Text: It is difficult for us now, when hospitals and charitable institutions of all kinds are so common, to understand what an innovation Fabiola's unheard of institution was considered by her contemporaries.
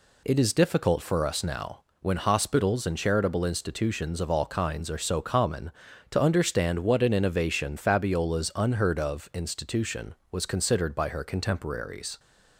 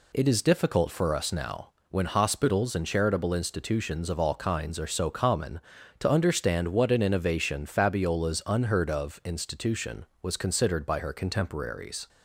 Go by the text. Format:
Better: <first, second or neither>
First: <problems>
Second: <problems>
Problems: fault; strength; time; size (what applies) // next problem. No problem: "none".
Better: neither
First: none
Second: none